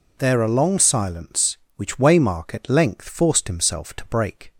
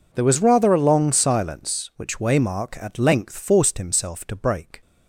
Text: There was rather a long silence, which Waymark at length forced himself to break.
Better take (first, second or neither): second